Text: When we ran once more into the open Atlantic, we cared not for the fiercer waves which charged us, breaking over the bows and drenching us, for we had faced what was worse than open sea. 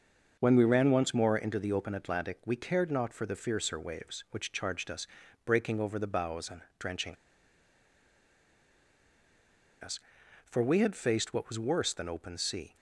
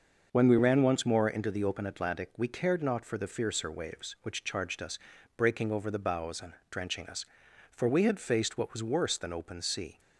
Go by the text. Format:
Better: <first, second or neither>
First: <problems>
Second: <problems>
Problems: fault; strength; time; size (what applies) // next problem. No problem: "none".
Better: second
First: starts louder than the rest; until 1.4 s; 6.5 dB // pauses between "and" and "drenching"; slight; at 6.5 s; 0.18 s long // pauses between "drenching" and "us"; strong; at 7.1 s; 2.6 s long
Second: starts louder than the rest; until 1.3 s; 6.5 dB // pauses between "and" and "drenching"; slight; at 6.5 s; 0.18 s long